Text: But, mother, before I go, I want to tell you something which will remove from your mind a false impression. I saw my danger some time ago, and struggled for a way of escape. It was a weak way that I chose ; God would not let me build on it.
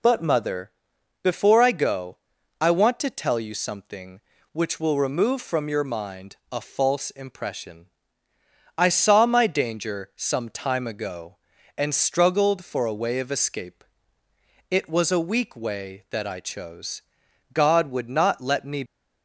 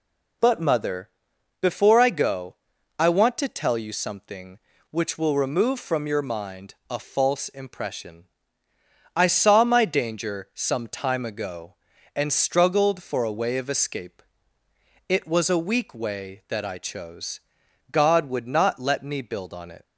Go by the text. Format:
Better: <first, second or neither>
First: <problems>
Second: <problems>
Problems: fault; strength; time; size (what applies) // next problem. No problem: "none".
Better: second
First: pauses between "mind" and "a"; slight; at 6.3 s; 0.16 s long // stops before "build on it"; at 18.8 s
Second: pauses between "mind" and "a"; slight; at 6.7 s; 0.16 s long